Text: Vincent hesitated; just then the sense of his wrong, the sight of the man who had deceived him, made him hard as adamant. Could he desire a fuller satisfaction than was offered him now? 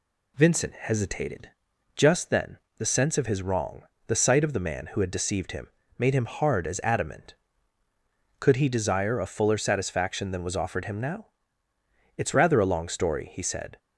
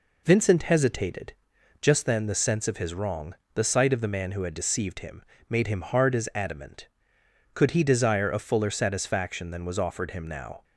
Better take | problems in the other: second | pauses between "then" and "the"; slight; at 2.5 s; 0.20 s long // goes on to say "It's rather a long story he said"; from 12.1 s on; 1.6 s long

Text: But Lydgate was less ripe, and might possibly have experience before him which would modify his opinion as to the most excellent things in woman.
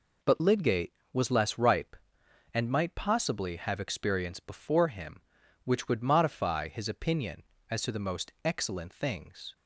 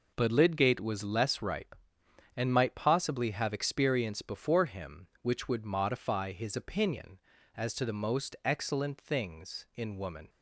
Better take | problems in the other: second | stops before "in woman"; at 9.5 s

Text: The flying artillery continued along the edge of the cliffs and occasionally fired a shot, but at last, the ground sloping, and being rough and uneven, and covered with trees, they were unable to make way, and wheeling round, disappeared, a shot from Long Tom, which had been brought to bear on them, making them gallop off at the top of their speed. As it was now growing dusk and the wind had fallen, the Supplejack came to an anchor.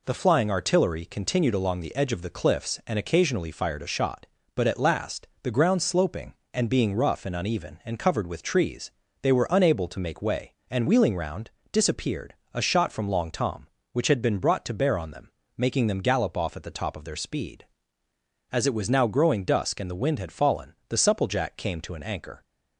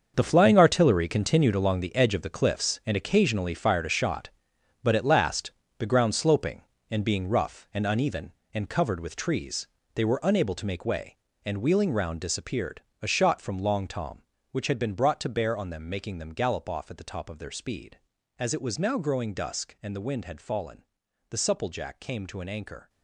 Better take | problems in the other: first | gets quieter; strong; throughout; 12 dB

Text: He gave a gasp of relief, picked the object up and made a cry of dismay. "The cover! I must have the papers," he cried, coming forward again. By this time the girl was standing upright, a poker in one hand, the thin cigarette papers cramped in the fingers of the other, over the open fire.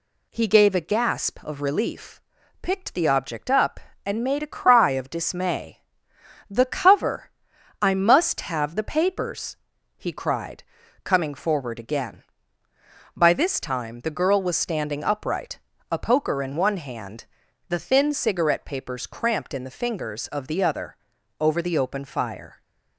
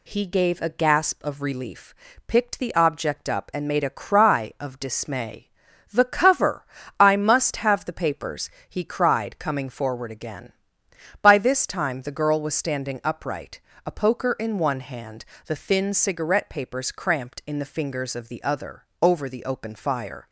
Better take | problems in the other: neither | none

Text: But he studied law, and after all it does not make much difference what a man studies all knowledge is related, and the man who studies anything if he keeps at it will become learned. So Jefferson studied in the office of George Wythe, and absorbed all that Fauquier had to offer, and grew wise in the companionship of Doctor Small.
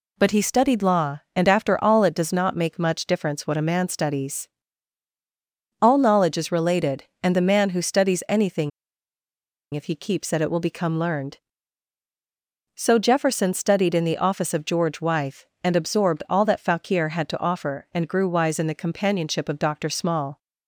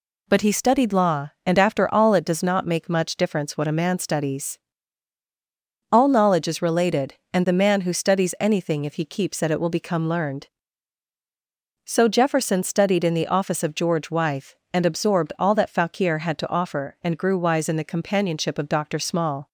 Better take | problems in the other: second | pauses between "studies" and "all"; strong; at 4.4 s; 1.3 s long; strong in the second // pauses between "anything" and "if"; at 8.7 s; 1.0 s long

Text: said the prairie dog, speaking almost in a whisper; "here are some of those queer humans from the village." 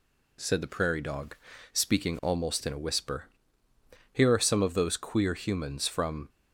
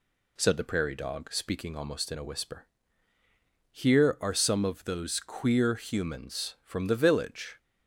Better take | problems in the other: second | stops before "the village"; at 6.2 s

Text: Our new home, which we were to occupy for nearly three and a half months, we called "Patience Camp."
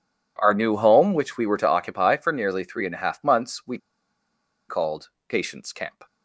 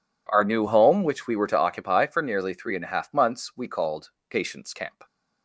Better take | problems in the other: second | pauses between "we" and "called"; noticeable; at 3.7 s; 0.89 s long // pauses between "called" and "Patience"; slight; at 5.0 s; 0.18 s long; slight in the second

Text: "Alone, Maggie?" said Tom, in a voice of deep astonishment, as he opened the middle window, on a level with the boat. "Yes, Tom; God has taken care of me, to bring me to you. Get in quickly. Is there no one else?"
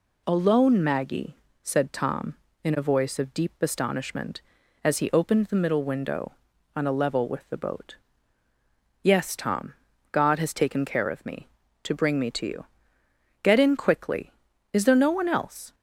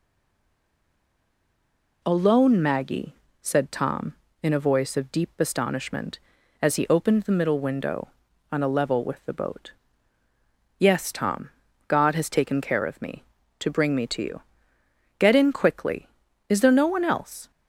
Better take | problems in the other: first | stays silent before the first word; noticeable; until 2.0 s; 2.0 s long

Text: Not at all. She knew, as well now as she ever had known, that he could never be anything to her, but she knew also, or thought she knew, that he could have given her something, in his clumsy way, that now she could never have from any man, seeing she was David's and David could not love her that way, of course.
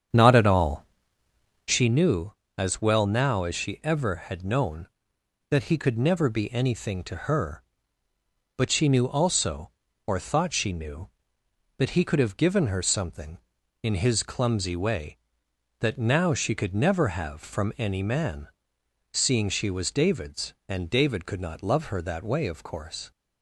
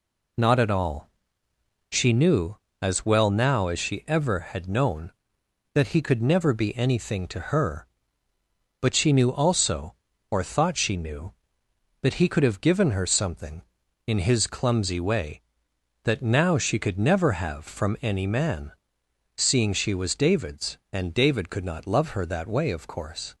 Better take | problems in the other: second | starts louder than the rest; strong; until 1.8 s; 8 dB

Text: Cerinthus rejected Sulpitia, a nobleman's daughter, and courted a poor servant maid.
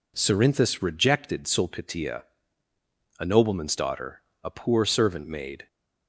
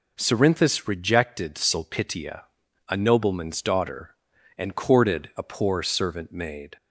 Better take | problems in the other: second | skips "and courted"; at 4.3 s

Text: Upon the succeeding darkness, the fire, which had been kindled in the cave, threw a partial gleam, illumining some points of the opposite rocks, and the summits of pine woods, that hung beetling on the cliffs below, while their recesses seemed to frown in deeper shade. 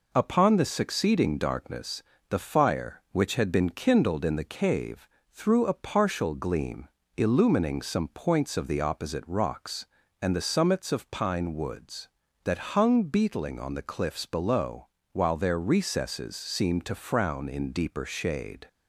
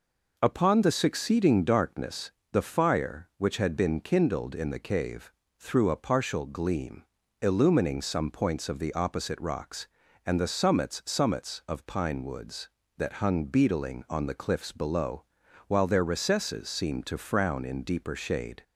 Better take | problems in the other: first | says "summits" twice; at 11.0 s

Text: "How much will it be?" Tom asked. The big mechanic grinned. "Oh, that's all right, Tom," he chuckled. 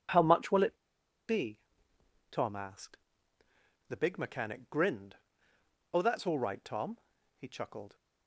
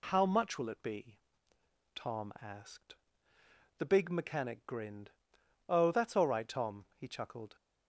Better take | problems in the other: second | pauses between "it" and "be"; noticeable; at 0.7 s; 0.53 s long

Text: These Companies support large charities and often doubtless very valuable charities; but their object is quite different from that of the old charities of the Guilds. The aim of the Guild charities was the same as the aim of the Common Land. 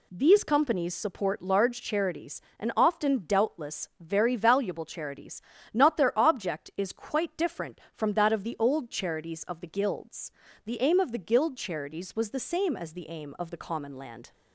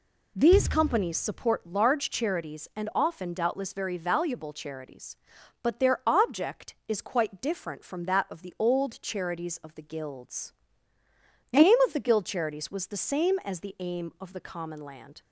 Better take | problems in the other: second | says "not" for "but"; at 5.7 s

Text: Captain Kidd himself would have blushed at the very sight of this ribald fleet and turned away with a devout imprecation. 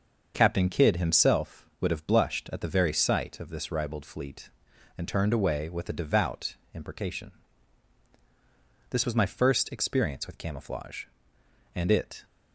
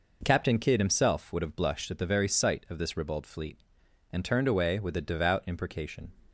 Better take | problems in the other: second | starts louder than the rest; until 1.3 s; 6.5 dB // pauses between "devout" and "imprecation"; slight; at 6.5 s; 0.16 s long // goes on to say "This was my first experience with camouflage and it"; strong; from 8.8 s on; 3.3 s long

